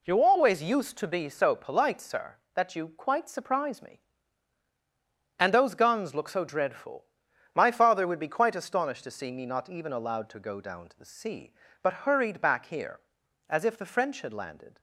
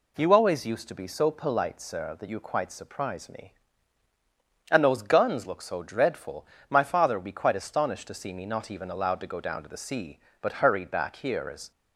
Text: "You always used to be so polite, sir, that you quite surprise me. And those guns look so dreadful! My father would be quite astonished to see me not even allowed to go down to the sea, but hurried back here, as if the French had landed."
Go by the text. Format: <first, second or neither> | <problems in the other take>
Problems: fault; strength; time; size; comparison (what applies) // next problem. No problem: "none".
first | stops before "if the French had landed"; at 11.7 s